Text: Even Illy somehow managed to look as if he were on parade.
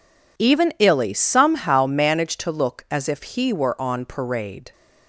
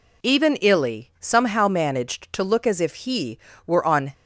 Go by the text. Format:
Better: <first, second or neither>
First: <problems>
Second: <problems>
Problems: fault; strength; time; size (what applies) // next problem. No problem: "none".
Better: first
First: none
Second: stops before "parade"; at 4.1 s